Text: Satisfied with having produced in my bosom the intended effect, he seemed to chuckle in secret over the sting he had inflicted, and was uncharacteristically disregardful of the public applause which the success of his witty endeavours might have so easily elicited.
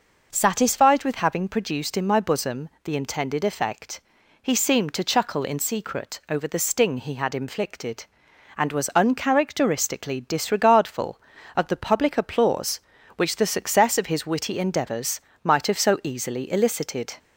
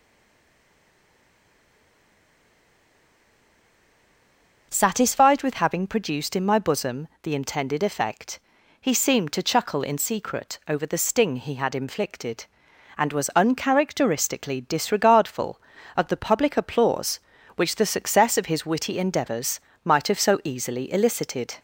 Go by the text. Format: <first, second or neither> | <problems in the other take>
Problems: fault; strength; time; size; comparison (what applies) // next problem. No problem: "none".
first | stays silent before the first word; strong; until 4.7 s; 4.7 s long // pauses between "bosom" and "the"; slight; at 7.0 s; 0.16 s long; slight in the first // pauses between "endeavours" and "might"; slight; at 19.5 s; 0.24 s long; slight in the first